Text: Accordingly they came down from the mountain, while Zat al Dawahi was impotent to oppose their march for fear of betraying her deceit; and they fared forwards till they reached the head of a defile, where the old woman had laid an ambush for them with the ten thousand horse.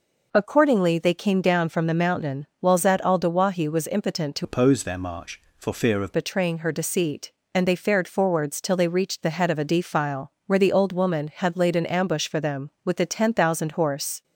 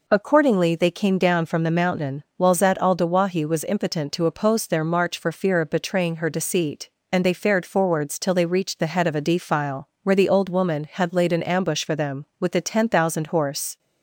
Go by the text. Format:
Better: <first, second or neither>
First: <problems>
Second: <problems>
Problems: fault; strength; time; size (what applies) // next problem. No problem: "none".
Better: second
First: changes voice from "oppose" to "of"; from 4.4 to 6.1 s; 1.7 s long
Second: none